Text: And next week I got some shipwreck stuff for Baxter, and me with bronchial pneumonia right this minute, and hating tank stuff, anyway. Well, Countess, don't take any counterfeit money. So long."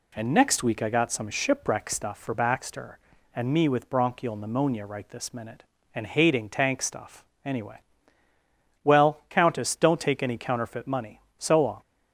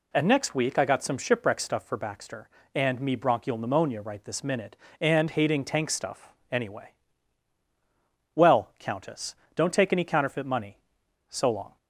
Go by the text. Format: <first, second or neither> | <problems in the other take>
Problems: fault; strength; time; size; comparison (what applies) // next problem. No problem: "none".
first | skips "with"; at 3.1 s